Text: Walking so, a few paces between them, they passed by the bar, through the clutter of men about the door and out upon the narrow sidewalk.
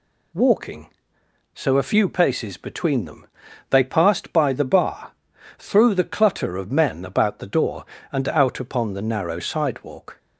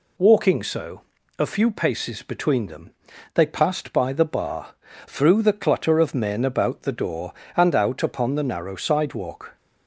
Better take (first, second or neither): neither